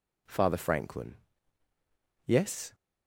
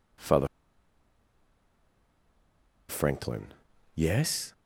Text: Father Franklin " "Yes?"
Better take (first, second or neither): first